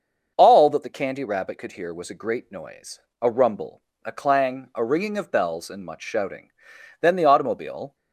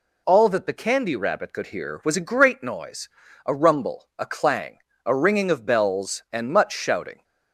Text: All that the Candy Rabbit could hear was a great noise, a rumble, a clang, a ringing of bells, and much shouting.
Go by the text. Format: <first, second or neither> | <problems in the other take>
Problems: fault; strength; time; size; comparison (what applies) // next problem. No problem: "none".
second | starts louder than the rest; until 1.3 s; 6.5 dB // goes on to say "Then the automobile"; noticeable; from 7.0 s on; 0.94 s long